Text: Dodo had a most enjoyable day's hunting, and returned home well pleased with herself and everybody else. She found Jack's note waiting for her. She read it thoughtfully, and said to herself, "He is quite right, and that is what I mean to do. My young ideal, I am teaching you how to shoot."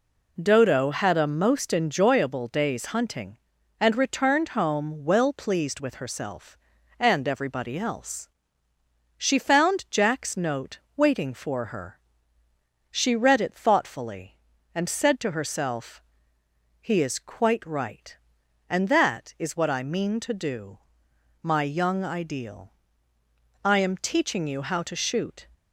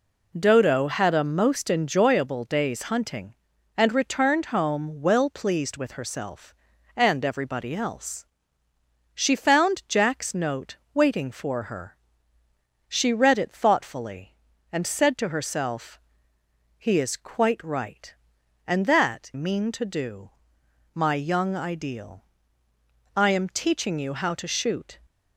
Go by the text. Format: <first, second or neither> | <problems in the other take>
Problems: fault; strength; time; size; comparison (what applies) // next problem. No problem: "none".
first | pauses between "note" and "waiting"; slight; at 10.7 s; 0.18 s long; slight in the first // skips "is what I"; at 19.3 s